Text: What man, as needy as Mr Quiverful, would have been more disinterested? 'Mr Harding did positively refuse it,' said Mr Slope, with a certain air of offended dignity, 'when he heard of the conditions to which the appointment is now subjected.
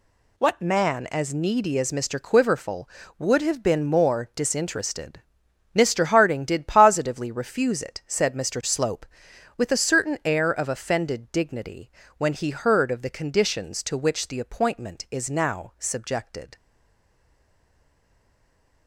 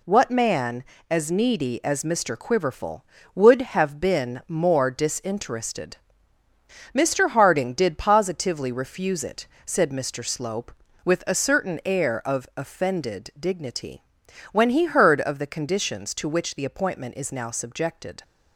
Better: second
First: stays silent after the last word; from 16.5 s on; 2.3 s long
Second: none

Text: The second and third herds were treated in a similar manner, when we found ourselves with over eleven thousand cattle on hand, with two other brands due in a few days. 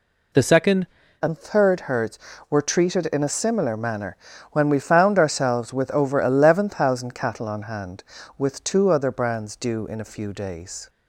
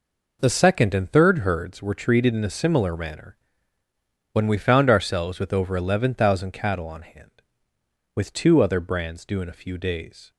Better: second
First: changes voice at "and"; from 1.2 s on; 9.6 s long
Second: none

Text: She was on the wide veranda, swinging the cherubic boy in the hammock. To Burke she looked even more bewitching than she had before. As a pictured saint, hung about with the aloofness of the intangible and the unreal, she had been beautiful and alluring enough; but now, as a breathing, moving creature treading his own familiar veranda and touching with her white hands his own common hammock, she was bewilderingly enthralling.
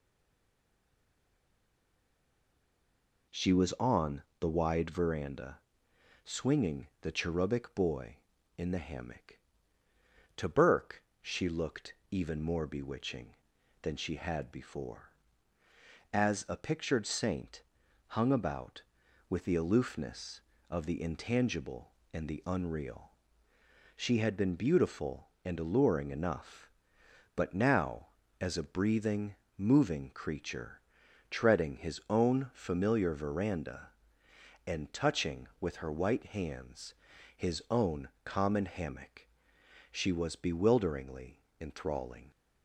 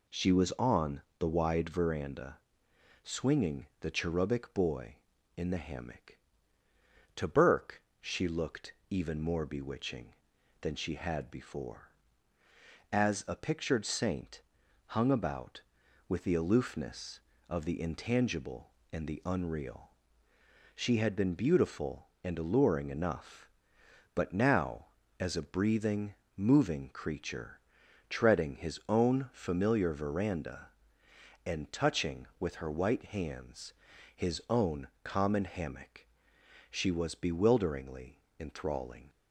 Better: second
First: stays silent before the first word; strong; until 3.3 s; 3.3 s long // pauses between "on" and "the"; slight; at 4.2 s; 0.18 s long // pauses between "swinging" and "the"; slight; at 6.8 s; 0.16 s long // pauses between "Burke" and "she"; slight; at 11.0 s; 0.18 s long // pauses between "looked" and "even"; slight; at 11.9 s; 0.16 s long // pauses between "creature" and "treading"; noticeable; at 30.8 s; 0.50 s long // pauses between "hands" and "his"; at 36.9 s; 0.42 s long // pauses between "own" and "common"; slight; at 38.0 s; 0.16 s long // pauses between "bewilderingly" and "enthralling"; slight; at 41.3 s; 0.22 s long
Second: pauses between "on" and "the"; slight; at 1.0 s; 0.18 s long // pauses between "swinging" and "the"; slight; at 3.6 s; 0.16 s long // pauses between "Burke" and "she"; slight; at 7.8 s; 0.18 s long // pauses between "looked" and "even"; slight; at 8.7 s; 0.16 s long // pauses between "creature" and "treading"; noticeable; at 27.5 s; 0.50 s long // pauses between "hands" and "his"; at 33.7 s; 0.42 s long // pauses between "own" and "common"; slight; at 34.8 s; 0.16 s long // pauses between "bewilderingly" and "enthralling"; slight; at 38.1 s; 0.22 s long

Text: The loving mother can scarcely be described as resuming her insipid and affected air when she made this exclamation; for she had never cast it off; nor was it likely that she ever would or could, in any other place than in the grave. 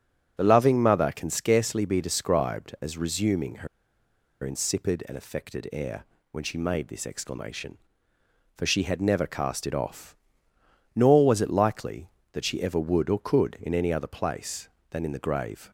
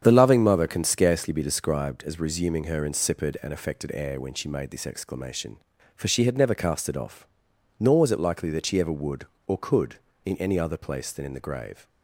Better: second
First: starts louder than the rest; strong; until 1.4 s; 7.5 dB // pauses between "her" and "insipid"; noticeable; at 3.6 s; 0.76 s long // pauses between "air" and "when"; slight; at 6.0 s; 0.28 s long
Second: starts louder than the rest; strong; until 1.0 s; 8 dB

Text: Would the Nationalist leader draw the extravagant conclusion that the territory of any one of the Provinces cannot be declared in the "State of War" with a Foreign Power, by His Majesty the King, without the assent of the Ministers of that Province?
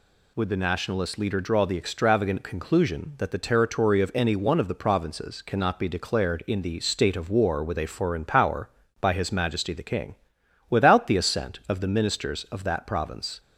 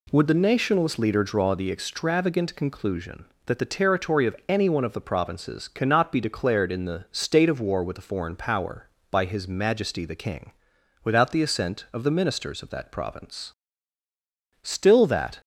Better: first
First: none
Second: goes on to say "Still that"; noticeable; from 14.6 s on; 0.78 s long

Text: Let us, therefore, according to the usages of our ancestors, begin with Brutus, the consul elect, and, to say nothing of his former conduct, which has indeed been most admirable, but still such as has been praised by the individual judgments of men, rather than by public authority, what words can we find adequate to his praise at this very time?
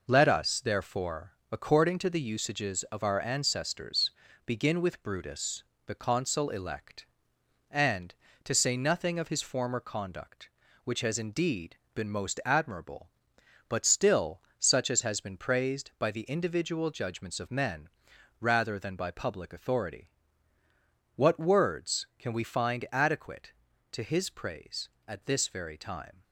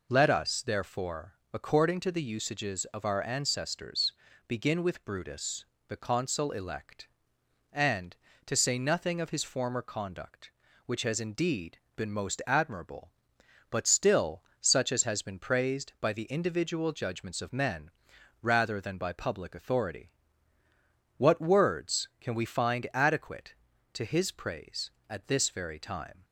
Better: second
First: gets quieter; throughout; 6.5 dB // pauses between "indeed" and "been"; slight; at 11.7 s; 0.18 s long // pauses between "still" and "such"; slight; at 14.4 s; 0.18 s long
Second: pauses between "indeed" and "been"; slight; at 11.7 s; 0.18 s long // pauses between "still" and "such"; slight; at 14.4 s; 0.18 s long

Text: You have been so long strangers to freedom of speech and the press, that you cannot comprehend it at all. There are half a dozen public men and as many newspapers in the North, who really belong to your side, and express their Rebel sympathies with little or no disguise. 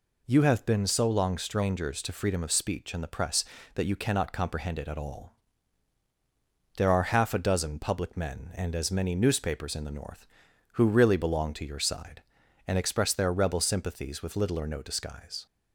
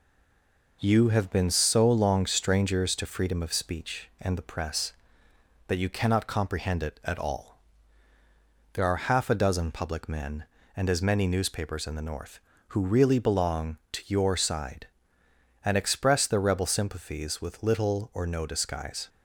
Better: first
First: none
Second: stays silent before the first word; slight; until 0.8 s; 0.8 s long

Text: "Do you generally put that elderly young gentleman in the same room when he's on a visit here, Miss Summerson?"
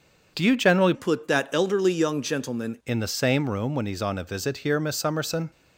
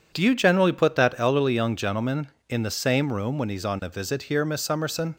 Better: second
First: starts louder than the rest; until 1.3 s; 6.5 dB // changes voice from "put" to "gentleman"; from 0.9 to 2.7 s; 1.8 s long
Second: none

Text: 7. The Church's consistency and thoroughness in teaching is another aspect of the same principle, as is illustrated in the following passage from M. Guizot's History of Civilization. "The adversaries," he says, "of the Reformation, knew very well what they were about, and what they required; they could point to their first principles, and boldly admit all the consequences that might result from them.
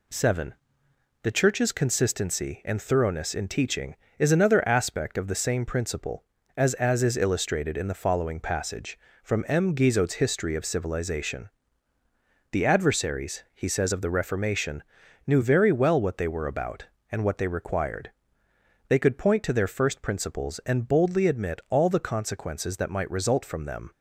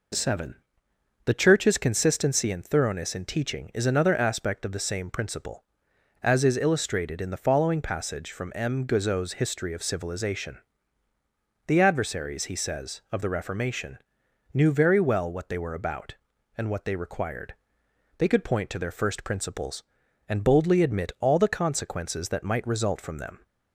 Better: second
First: says "as" twice; at 6.7 s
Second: none

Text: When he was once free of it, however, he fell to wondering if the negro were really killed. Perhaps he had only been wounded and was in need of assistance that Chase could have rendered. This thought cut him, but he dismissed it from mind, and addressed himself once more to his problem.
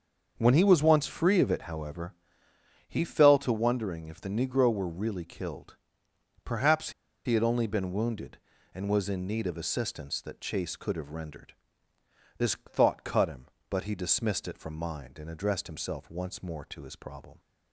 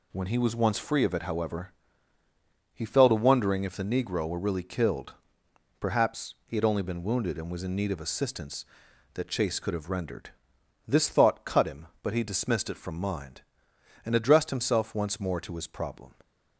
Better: second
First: starts louder than the rest; until 1.3 s; 6.5 dB // pauses between "Perhaps" and "he"; slight; at 6.9 s; 0.34 s long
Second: none

